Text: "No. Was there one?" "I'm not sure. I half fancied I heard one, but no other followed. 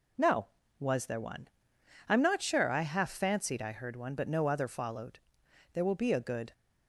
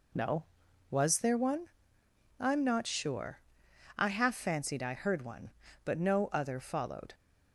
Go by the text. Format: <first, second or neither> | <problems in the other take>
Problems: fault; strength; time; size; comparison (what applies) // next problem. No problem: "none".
second | goes on to say "There will be a good"; noticeable; from 5.7 s on; 0.80 s long